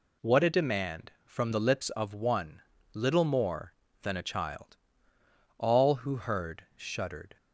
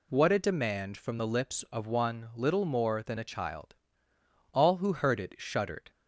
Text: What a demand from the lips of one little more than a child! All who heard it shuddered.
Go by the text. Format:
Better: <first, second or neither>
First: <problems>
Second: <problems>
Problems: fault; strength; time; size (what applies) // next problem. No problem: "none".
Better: second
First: pauses between "one" and "little"; slight; at 2.6 s; 0.32 s long // skips "it"; at 6.6 s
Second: none